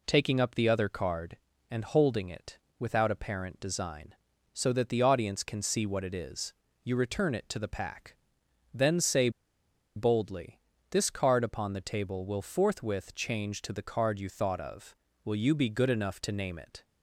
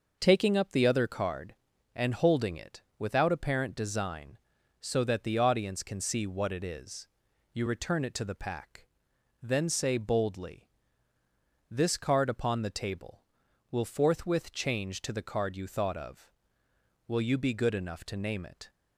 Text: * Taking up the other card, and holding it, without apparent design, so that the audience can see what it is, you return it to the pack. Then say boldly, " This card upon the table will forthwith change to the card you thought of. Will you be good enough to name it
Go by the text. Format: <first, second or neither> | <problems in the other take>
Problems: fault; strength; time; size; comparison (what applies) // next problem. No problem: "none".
second | pauses between "say" and "boldly"; noticeable; at 9.2 s; 0.66 s long